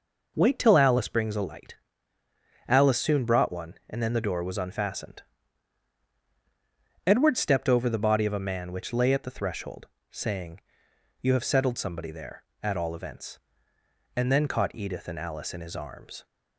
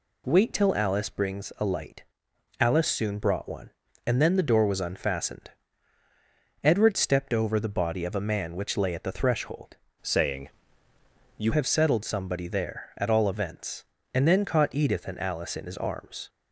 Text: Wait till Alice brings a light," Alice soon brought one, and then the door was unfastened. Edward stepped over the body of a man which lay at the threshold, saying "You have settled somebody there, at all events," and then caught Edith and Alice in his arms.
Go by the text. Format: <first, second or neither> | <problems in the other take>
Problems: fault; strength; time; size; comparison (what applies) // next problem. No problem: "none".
first | changes voice from "saying" to "You"; from 10.0 to 11.5 s; 1.5 s long // pauses between "saying" and "You"; noticeable; at 10.4 s; 0.90 s long; noticeable in the first